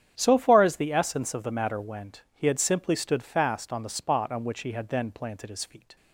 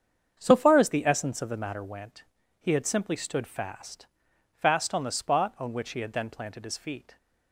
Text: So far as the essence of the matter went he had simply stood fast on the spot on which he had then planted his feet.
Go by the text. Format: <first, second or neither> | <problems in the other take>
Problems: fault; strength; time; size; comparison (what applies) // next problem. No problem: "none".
first | starts louder than the rest; strong; until 1.3 s; 7.5 dB; strong in the first // pauses between "went" and "he"; at 2.2 s; 0.38 s long // says "fast" twice; at 4.5 s